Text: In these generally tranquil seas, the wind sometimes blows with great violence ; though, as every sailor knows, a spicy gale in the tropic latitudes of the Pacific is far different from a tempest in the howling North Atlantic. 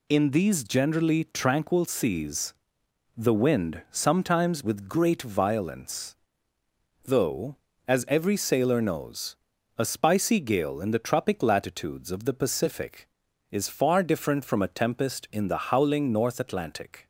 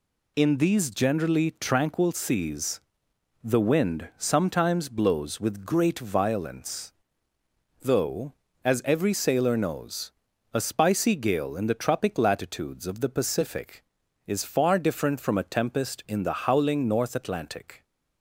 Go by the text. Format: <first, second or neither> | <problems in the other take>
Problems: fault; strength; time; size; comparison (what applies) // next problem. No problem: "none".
second | skips "blows"; at 4.6 s